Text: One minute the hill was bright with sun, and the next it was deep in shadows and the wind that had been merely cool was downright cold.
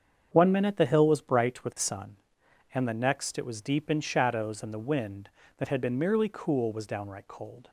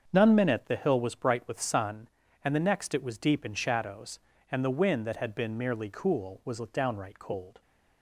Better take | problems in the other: first | starts louder than the rest; until 1.1 s; 6.5 dB; strong in the first // says "None" for "One"; at 0.1 s

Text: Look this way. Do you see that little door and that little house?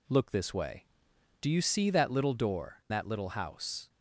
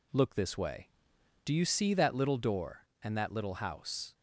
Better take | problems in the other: second | skips "and"; at 2.8 s

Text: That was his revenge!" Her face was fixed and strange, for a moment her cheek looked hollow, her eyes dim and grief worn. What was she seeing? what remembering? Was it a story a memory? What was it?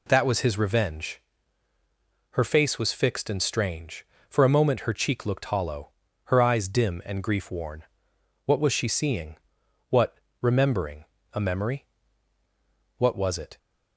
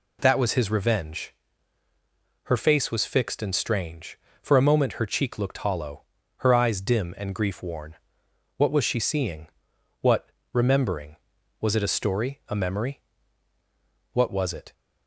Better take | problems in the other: second | pauses between "what" and "remembering"; slight; at 10.1 s; 0.24 s long; slight in the second // skips "Was it a story"; at 11.1 s

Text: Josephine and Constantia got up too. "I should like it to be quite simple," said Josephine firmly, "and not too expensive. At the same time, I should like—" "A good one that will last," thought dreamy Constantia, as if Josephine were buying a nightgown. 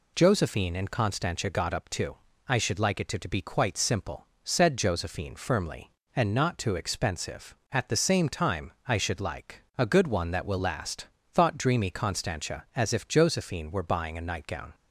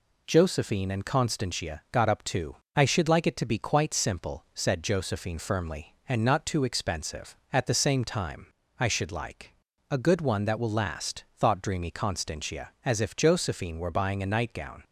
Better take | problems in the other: second | says "to" twice; at 3.1 s

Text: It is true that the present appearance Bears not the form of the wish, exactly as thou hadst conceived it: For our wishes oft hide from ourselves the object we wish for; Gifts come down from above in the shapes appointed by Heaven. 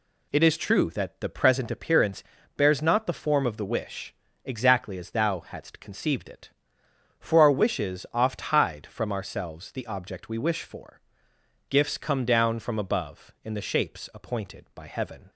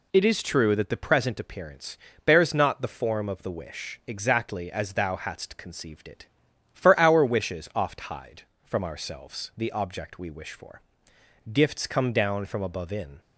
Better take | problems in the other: first | pauses between "appearance" and "Bears"; slight; at 1.9 s; 0.30 s long; slight in the first // stops before "the shapes appointed by Heaven"; at 13.2 s

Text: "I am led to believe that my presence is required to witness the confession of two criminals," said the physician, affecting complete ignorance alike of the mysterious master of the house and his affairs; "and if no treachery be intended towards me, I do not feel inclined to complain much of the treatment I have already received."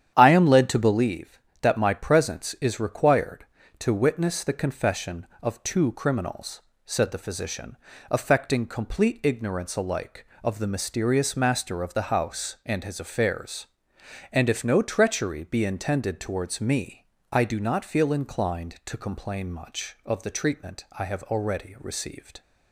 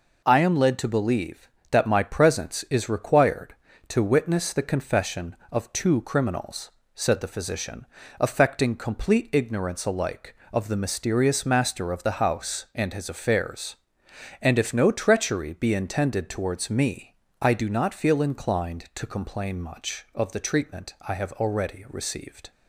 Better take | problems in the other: second | starts louder than the rest; strong; until 1.1 s; 9.5 dB

